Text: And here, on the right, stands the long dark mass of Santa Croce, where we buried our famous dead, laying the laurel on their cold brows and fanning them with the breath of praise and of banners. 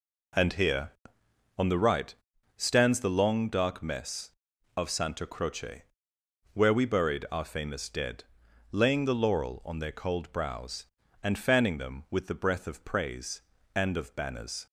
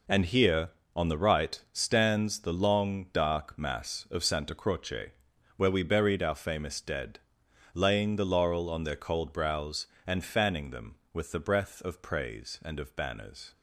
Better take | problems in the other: second | says "mess" for "mass"; at 3.8 s

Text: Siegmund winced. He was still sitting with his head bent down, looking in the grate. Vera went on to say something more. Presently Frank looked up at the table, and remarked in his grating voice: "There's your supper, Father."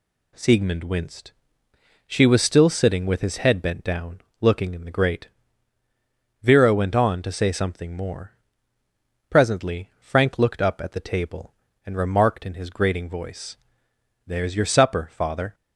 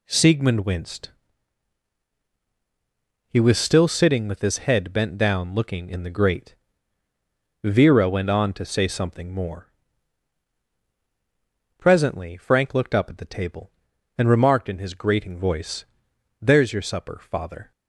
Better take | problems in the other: second | says "She" for "He"; at 2.0 s

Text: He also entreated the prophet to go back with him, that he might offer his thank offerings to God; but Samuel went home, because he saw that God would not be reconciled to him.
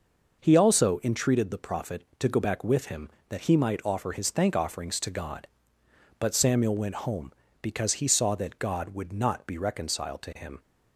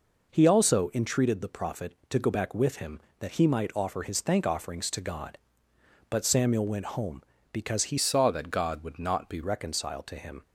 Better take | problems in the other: first | changes voice from "saw" to "be"; from 7.9 to 9.4 s; 1.5 s long

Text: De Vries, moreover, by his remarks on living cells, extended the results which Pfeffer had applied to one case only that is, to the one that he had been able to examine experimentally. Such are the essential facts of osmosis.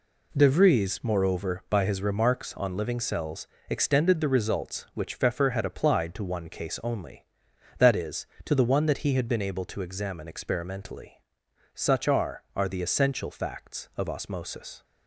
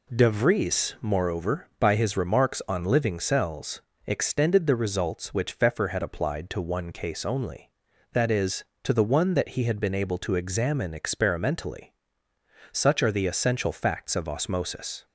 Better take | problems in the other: second | says "are" twice; at 12.5 s

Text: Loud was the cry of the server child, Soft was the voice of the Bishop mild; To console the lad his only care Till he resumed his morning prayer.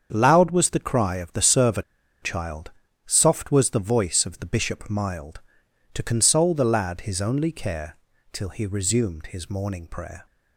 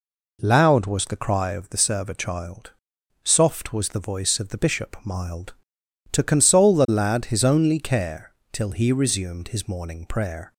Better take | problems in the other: second | starts louder than the rest; until 1.1 s; 7 dB // pauses between "server" and "child"; at 1.8 s; 0.40 s long // pauses between "care" and "Till"; slight; at 7.9 s; 0.34 s long; slight in the second

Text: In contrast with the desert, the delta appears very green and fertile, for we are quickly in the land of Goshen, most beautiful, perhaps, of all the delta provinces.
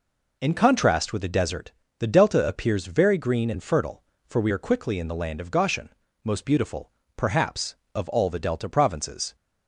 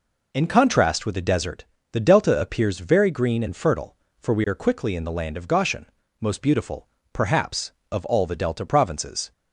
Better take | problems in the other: neither | none

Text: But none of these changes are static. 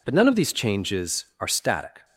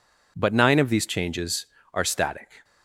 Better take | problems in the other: first | says "nine" for "none"; at 0.5 s

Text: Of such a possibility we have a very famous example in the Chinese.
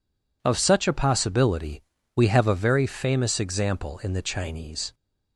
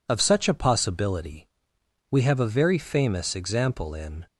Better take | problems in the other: first | pauses between "possibility" and "we"; noticeable; at 1.4 s; 0.64 s long; slight in the first // stops before "the Chinese"; at 4.2 s

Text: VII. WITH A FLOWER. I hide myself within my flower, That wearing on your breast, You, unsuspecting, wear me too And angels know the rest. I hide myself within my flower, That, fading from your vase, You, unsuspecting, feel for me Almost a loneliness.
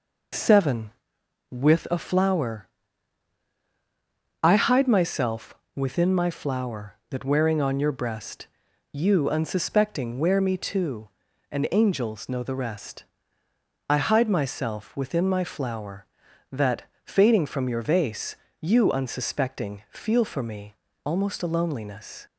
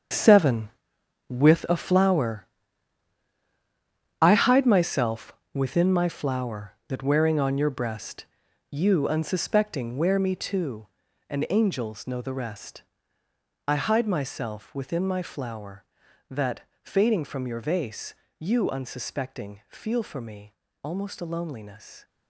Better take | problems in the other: first | gets quieter; strong; throughout; 11.5 dB // pauses between "myself" and "within"; slight; at 5.3 s; 0.22 s long; slight in the first // pauses between "me" and "Almost"; slight; at 20.5 s; 0.32 s long; slight in the first

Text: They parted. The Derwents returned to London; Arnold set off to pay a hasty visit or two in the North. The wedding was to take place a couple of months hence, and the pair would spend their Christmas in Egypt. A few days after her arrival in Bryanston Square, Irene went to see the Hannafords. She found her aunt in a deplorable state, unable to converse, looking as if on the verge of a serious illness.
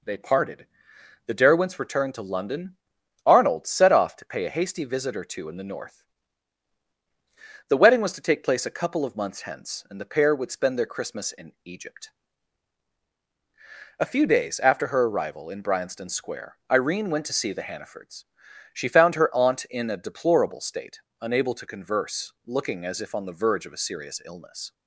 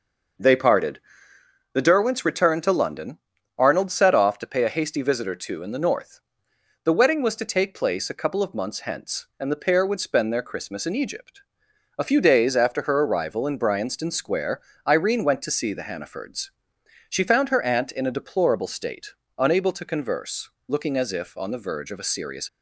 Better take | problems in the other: first | stops before "illness"; at 22.4 s

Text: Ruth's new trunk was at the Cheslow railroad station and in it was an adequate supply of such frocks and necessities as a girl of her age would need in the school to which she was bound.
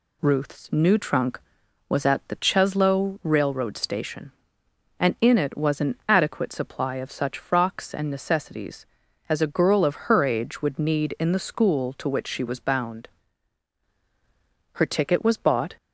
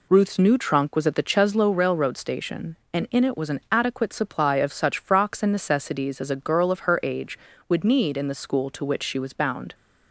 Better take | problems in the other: second | pauses between "an" and "adequate"; slight; at 5.9 s; 0.16 s long // goes on to say "Her ticket was bought"; noticeable; from 14.7 s on; 1.0 s long

